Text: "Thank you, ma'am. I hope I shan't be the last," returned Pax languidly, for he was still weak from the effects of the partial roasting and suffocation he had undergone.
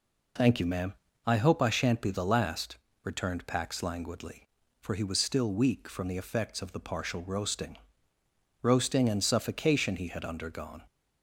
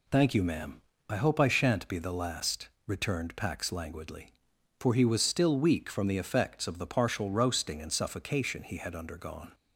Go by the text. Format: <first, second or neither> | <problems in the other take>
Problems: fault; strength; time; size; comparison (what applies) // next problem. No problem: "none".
second | says "roasting" twice; at 8.6 s